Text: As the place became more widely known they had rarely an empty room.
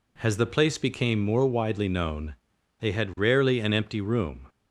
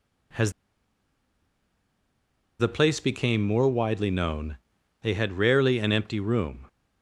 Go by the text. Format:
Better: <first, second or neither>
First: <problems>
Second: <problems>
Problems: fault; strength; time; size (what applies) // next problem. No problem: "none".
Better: first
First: pauses between "known" and "they"; at 2.3 s; 0.44 s long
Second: pauses between "As" and "the"; strong; at 0.5 s; 2.0 s long // pauses between "known" and "they"; at 4.5 s; 0.44 s long